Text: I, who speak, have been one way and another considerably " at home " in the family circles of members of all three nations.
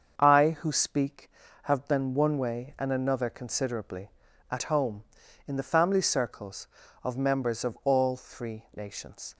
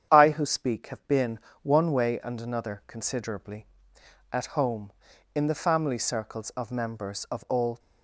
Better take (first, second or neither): first